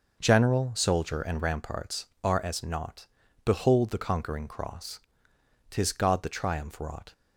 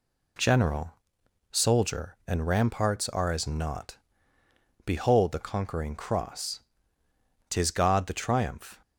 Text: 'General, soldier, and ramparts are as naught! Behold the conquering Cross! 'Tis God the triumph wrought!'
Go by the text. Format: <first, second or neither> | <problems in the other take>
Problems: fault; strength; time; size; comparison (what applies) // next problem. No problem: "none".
first | stops before "wrought"; at 8.8 s